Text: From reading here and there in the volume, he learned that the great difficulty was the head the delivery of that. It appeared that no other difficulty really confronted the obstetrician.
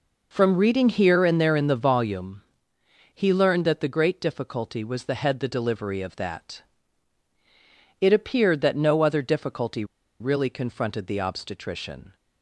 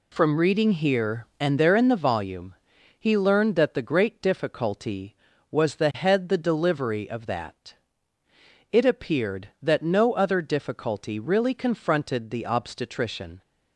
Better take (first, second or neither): second